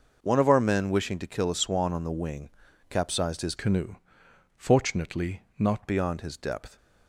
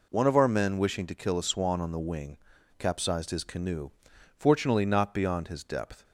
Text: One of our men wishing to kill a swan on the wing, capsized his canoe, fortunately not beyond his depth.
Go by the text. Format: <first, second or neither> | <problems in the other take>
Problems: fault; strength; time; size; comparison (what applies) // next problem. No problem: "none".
second | changes voice from "canoe" to "not"; from 3.5 to 5.8 s; 2.3 s long // pauses between "fortunately" and "not"; slight; at 5.4 s; 0.16 s long